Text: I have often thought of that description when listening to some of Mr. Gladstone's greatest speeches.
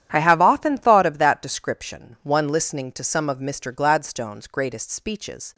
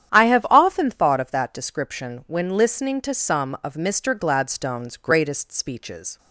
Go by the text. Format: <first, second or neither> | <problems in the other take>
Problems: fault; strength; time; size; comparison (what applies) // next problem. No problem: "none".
second | starts louder than the rest; strong; until 1.1 s; 10.5 dB; strong in the second // says "one" for "when"; at 2.2 s